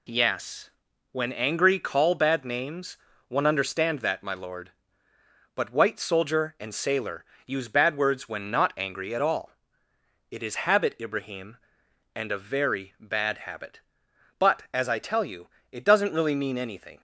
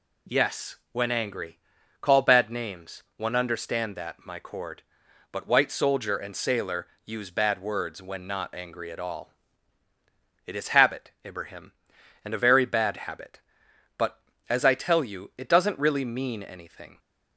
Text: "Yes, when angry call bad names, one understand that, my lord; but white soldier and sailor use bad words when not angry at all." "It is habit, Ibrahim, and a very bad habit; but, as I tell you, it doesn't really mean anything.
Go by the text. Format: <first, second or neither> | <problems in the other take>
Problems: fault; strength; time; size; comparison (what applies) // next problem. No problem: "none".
first | pauses between "angry" and "call"; at 1.5 s; 0.44 s long // says "cord" for "lord"; at 4.3 s // pauses between "sailor" and "use"; slight; at 6.8 s; 0.20 s long; slight in the first